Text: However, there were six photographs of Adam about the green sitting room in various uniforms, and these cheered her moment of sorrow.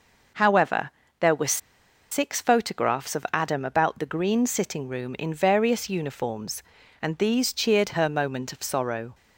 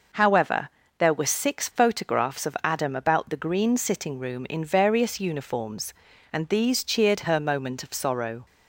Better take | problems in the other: second | pauses between "were" and "six"; noticeable; at 1.6 s; 0.52 s long

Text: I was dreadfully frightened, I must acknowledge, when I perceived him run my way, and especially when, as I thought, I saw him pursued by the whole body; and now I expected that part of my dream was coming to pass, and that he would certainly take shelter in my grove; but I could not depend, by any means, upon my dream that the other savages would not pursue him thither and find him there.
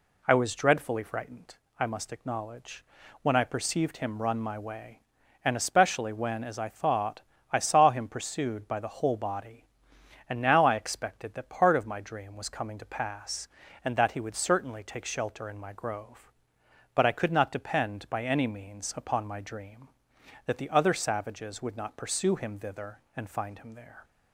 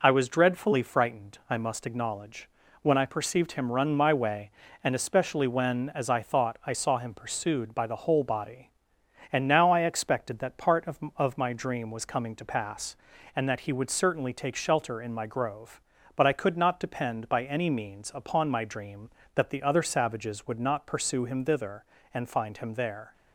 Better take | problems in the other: first | says "of" twice; at 11.1 s

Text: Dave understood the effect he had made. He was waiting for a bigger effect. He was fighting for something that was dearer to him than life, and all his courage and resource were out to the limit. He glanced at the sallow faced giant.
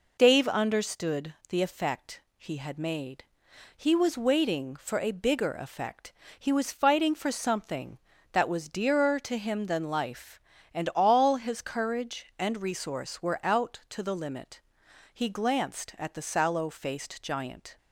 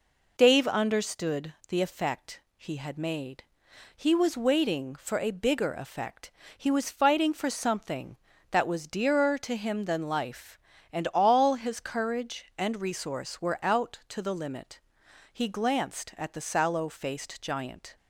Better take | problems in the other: neither | pauses between "understood" and "the"; slight; the same in both // pauses between "effect" and "he"; slight; the same in both

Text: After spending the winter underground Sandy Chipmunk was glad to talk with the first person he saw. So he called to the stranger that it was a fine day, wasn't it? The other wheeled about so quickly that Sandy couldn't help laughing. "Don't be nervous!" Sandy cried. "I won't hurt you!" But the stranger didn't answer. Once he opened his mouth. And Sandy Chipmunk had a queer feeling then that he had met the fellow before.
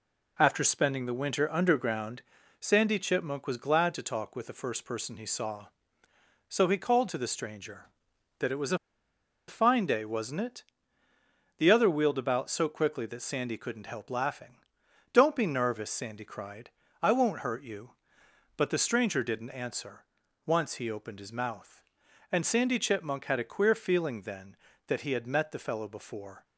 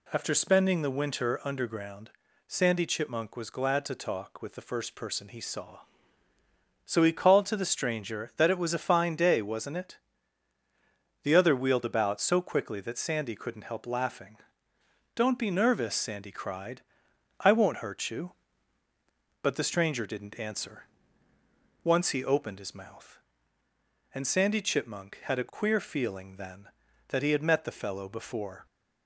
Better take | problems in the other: second | pauses between "underground" and "Sandy"; at 2.2 s; 0.38 s long; slight in the second // pauses between "a" and "fine"; noticeable; at 8.7 s; 0.70 s long

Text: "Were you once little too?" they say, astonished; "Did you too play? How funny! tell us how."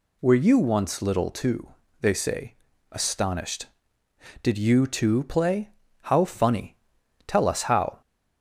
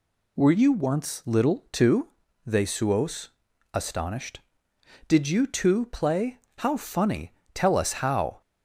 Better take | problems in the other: first | says "suos" for "say"; at 2.6 s

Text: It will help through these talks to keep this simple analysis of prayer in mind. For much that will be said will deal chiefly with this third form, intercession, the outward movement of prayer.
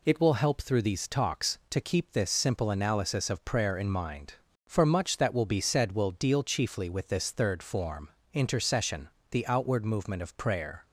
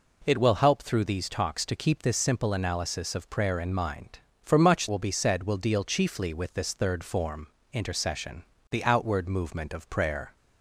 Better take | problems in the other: first | skips "that"; at 4.8 s

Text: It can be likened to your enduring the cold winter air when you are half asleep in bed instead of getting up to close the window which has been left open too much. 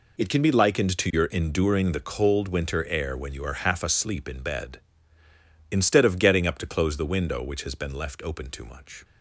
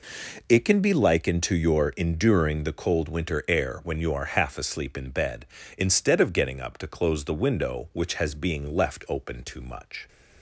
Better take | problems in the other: first | says "being" for "been"; at 8.3 s

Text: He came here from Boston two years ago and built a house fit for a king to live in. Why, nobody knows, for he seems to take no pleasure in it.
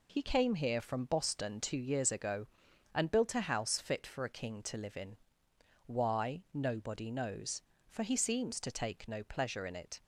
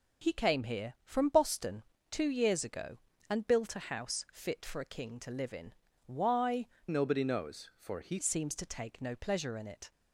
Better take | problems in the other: first | pauses between "Boston" and "two"; slight; at 1.8 s; 0.26 s long // changes voice from "nobody" to "he"; from 6.8 to 8.1 s; 1.3 s long

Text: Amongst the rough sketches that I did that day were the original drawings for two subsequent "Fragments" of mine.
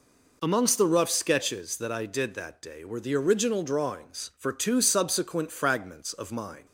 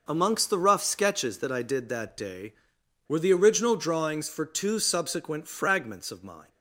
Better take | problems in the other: neither | none

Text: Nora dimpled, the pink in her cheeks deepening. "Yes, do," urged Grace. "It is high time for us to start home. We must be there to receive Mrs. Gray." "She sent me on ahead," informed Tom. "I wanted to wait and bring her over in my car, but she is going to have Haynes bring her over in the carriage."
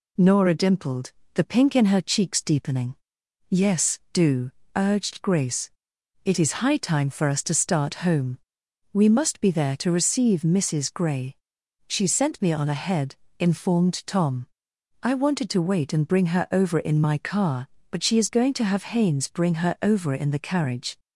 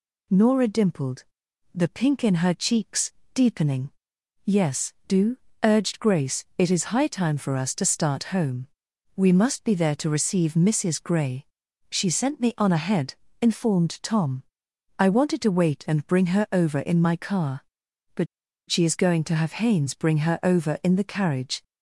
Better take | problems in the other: first | pauses between "cheeks" and "deepening"; slight; at 3.1 s; 0.22 s long // pauses between "but" and "she"; at 18.2 s; 0.42 s long

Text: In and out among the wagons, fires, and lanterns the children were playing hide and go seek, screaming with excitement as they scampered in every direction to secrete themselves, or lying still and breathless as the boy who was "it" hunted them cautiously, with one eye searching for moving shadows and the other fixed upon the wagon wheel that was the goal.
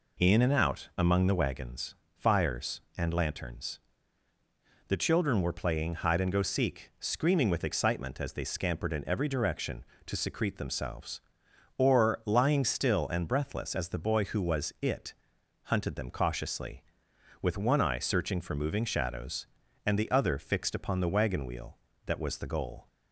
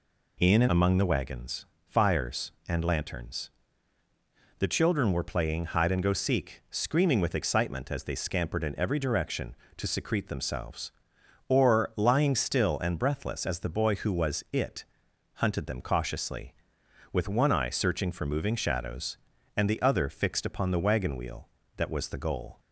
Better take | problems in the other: first | skips "out"; at 0.6 s // pauses between "lanterns" and "the"; at 3.4 s; 1.1 s long; also in the first // pauses between "it" and "hunted"; noticeable; at 14.8 s; 0.52 s long; noticeable in the first

